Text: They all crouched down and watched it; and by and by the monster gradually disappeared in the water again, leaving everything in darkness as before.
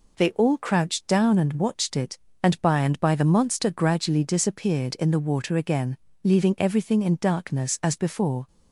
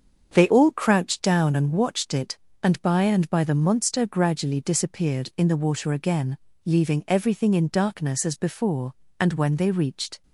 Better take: first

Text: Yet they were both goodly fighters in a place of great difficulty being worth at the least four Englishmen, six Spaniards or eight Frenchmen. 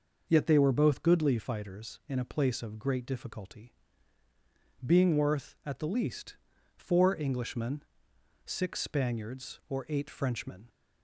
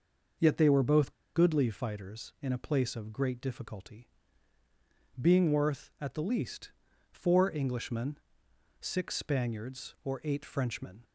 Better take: first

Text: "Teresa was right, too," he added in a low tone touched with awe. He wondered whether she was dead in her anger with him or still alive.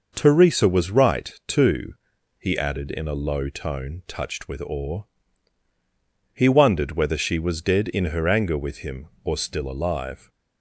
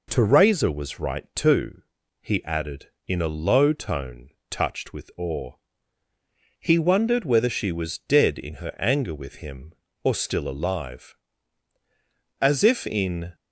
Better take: first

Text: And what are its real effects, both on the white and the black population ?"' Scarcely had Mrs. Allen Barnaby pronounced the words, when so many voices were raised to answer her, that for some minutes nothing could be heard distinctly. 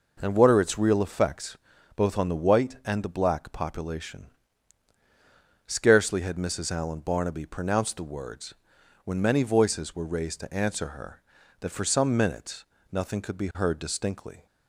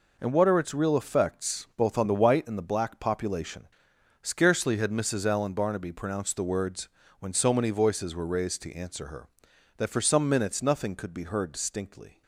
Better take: second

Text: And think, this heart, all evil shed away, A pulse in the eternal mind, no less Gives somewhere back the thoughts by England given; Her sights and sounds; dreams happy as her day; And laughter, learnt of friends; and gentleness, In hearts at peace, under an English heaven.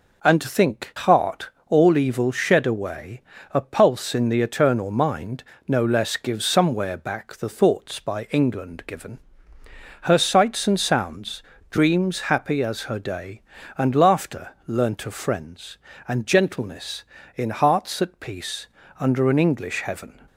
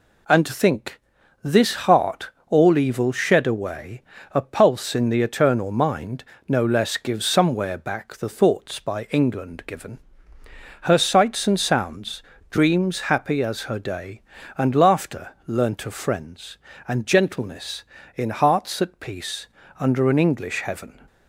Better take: second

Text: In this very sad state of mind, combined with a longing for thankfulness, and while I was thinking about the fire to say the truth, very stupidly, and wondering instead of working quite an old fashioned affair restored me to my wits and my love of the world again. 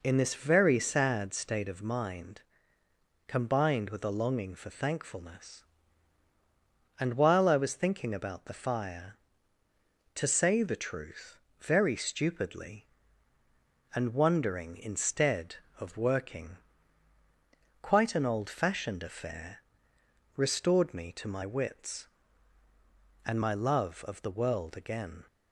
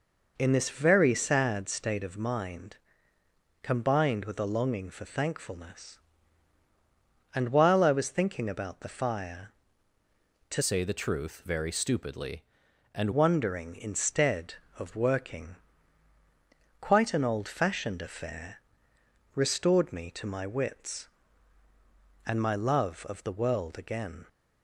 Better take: first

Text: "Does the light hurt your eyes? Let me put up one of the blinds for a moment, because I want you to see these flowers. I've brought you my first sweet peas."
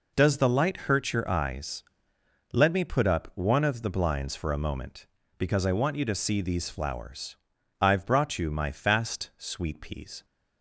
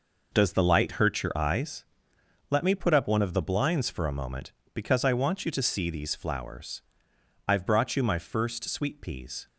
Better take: second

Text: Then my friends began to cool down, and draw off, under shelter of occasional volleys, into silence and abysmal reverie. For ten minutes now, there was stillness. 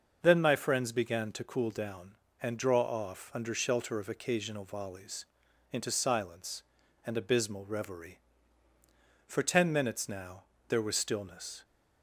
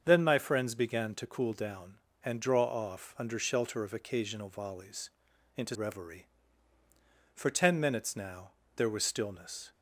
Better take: first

